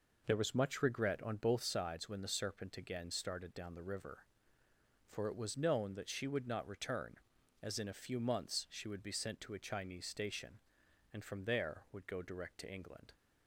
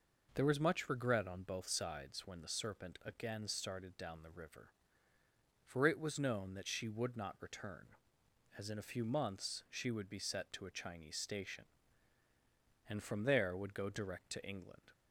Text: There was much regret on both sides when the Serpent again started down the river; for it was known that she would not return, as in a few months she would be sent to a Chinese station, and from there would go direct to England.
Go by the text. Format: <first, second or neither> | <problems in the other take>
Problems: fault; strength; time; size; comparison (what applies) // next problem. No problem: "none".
first | says "set" for "sent"; at 10.1 s